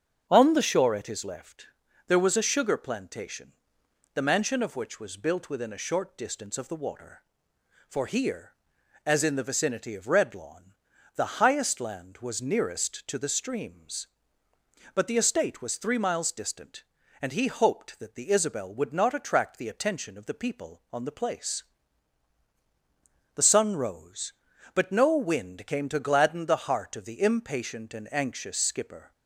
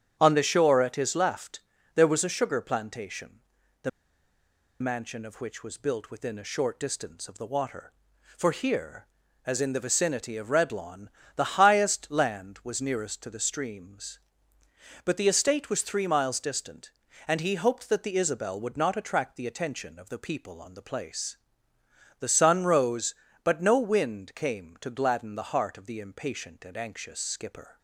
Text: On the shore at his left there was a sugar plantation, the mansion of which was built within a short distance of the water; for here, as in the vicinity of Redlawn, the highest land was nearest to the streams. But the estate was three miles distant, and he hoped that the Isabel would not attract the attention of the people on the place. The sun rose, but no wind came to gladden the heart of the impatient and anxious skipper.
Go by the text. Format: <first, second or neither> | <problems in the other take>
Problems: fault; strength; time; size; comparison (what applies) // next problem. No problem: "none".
first | starts louder than the rest; strong; until 1.2 s; 8.5 dB; strong in the first // pauses between "left" and "there"; slight; at 1.5 s; 0.34 s long; also in the first // pauses between "the" and "mansion"; noticeable; at 3.8 s; 0.91 s long